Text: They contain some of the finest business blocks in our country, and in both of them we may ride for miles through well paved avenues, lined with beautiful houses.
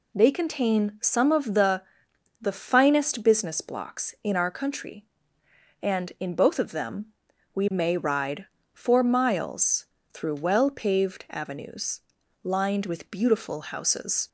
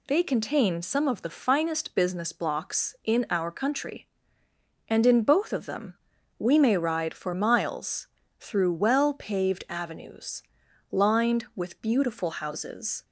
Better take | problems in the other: second | says "the" twice; at 2.4 s // pauses between "them" and "we"; noticeable; at 7.0 s; 0.48 s long; also in the second // pauses between "miles" and "through"; slight; at 9.8 s; 0.26 s long; slight in the second

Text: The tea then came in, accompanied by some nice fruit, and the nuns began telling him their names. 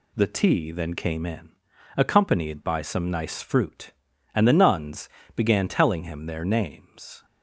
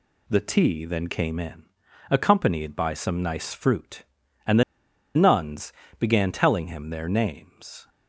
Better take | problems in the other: first | pauses between "the" and "nuns"; noticeable; at 4.6 s; 0.53 s long // pauses between "nuns" and "began"; slight; at 5.7 s; 0.26 s long; slight in the first

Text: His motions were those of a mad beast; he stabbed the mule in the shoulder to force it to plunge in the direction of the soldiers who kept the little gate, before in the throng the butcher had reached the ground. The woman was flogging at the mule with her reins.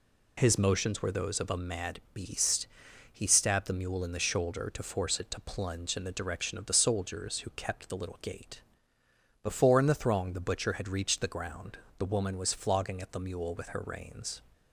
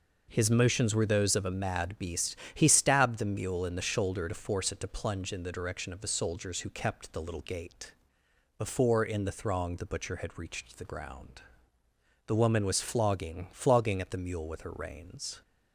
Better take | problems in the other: first | says "flogging" twice; at 13.5 s

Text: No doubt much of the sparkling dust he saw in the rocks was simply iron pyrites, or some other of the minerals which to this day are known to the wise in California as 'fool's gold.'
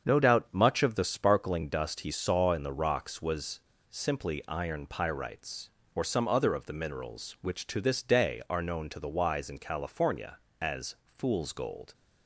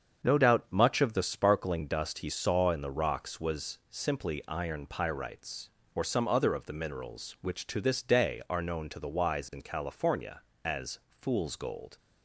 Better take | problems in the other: second | starts louder than the rest; strong; until 1.1 s; 7.5 dB; strong in the second // pauses between "was" and "simply"; slight; at 3.6 s; 0.28 s long

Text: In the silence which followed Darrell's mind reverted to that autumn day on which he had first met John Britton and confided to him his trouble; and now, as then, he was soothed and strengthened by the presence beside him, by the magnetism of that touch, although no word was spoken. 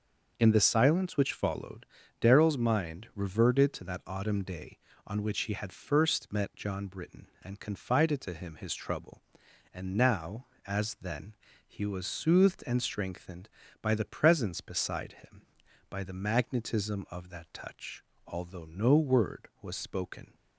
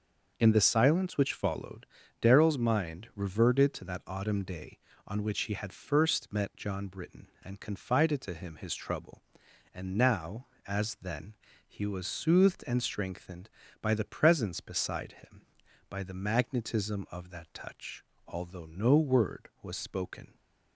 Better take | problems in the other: neither | pauses between "followed" and "Darrell's"; slight; the same in both

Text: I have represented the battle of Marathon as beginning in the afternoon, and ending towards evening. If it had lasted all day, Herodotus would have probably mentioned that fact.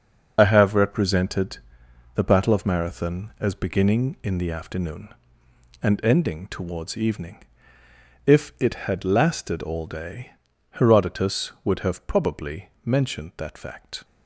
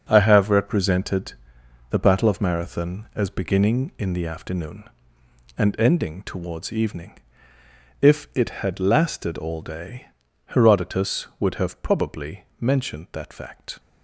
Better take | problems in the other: second | loses the start of "I"; at 0.3 s; 70 ms // starts louder than the rest; noticeable; until 1.3 s; 6 dB; also in the second // pauses between "represented" and "the"; noticeable; at 1.5 s; 0.56 s long; noticeable in the second

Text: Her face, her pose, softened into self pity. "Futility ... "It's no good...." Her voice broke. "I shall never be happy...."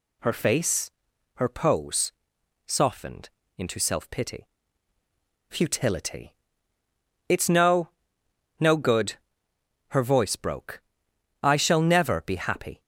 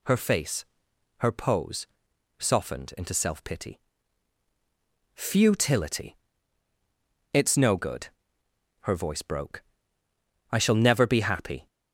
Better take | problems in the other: second | pauses between "softened" and "into"; slight; at 3.2 s; 0.28 s long // says "no" twice; at 8.5 s

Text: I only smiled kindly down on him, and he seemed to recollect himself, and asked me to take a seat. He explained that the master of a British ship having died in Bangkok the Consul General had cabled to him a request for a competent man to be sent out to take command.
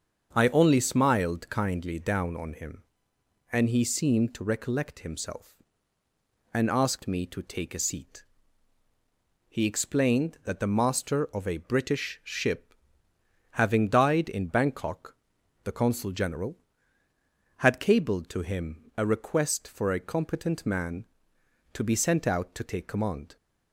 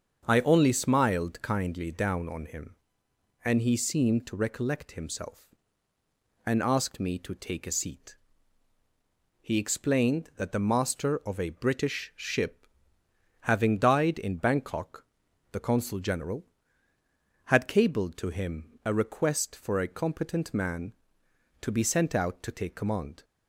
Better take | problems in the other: neither | starts louder than the rest; the same in both // pauses between "ship" and "having"; noticeable; the same in both // pauses between "Bangkok" and "the"; noticeable; the same in both

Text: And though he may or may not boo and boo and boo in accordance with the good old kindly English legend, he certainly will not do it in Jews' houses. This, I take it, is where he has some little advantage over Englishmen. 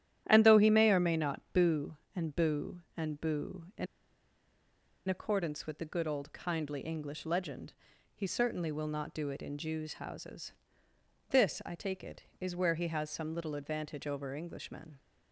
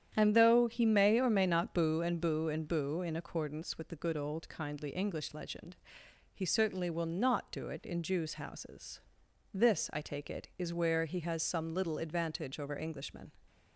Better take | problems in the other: second | starts louder than the rest; strong; until 1.2 s; 11.5 dB; strong in the second // pauses between "in" and "accordance"; at 3.8 s; 1.2 s long

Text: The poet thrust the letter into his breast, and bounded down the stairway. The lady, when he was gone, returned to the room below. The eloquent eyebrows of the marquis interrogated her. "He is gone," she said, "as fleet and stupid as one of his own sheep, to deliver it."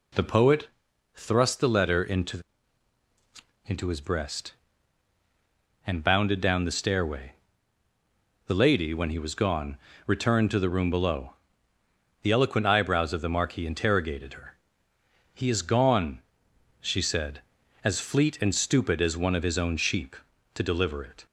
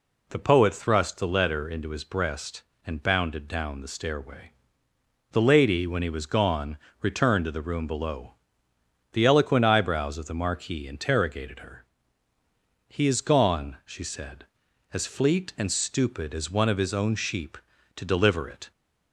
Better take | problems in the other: second | pauses between "poet" and "thrust"; noticeable; at 0.6 s; 0.48 s long // says "into" twice; at 3.6 s

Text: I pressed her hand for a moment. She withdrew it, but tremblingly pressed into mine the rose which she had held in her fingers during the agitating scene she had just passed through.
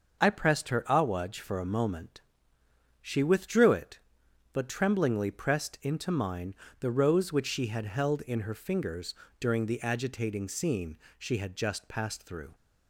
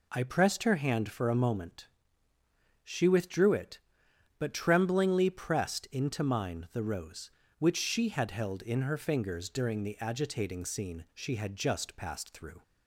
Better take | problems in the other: second | starts louder than the rest; until 1.2 s; 6 dB // says "awaj" for "hand"; at 0.8 s // pauses between "mine" and "the"; slight; at 6.5 s; 0.24 s long // pauses between "fingers" and "during"; slight; at 9.1 s; 0.26 s long // pauses between "scene" and "she"; slight; at 10.9 s; 0.22 s long

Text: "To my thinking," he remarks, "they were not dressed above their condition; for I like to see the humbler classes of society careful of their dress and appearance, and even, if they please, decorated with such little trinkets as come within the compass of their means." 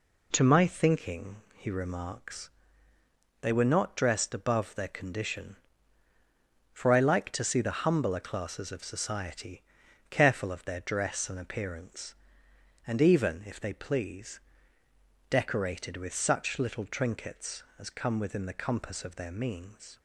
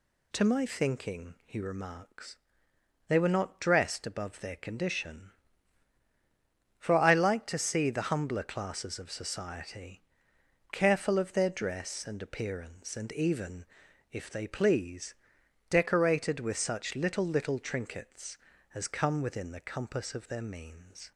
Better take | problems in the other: first | pauses between "society" and "careful"; noticeable; at 10.0 s; 0.70 s long; noticeable in the first // says "little" twice; at 17.2 s

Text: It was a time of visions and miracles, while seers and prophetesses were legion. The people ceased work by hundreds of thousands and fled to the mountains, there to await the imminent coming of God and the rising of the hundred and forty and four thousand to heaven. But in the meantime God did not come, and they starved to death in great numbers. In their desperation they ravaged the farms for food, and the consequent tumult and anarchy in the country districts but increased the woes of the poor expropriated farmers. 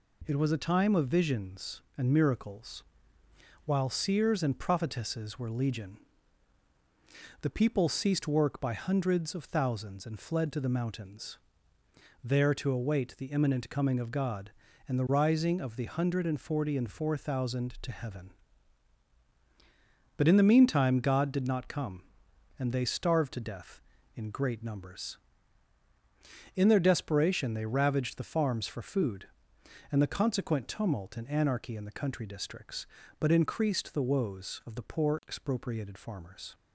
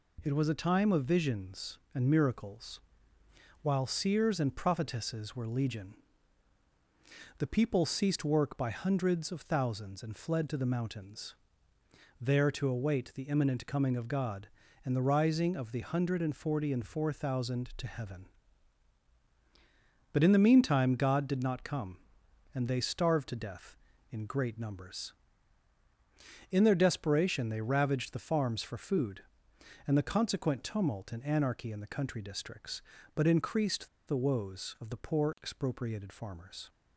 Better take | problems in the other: first | pauses between "increased" and "the"; slight; at 33.8 s; 0.19 s long

